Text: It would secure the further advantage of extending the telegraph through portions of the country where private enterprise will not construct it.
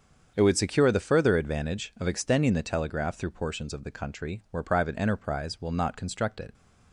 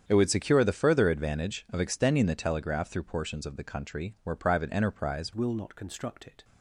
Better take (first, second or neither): first